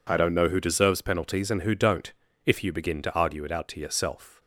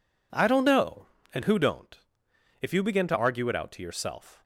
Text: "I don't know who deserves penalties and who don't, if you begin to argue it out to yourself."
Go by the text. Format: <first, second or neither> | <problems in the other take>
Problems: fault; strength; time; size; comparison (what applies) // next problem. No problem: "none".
first | skips "who deserves penalties"; at 1.2 s